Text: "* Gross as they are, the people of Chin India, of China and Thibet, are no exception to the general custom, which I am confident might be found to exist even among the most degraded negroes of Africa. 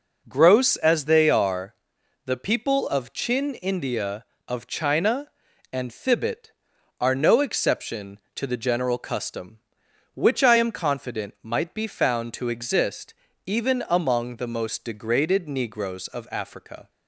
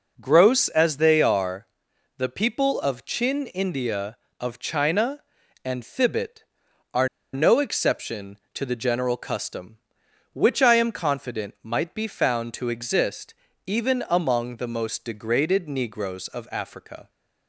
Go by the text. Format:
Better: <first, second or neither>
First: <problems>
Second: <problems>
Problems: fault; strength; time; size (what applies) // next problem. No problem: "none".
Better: first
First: pauses between "exist" and "even"; slight; at 13.1 s; 0.32 s long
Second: pauses between "are" and "no"; slight; at 7.0 s; 0.26 s long // pauses between "exist" and "even"; slight; at 13.3 s; 0.32 s long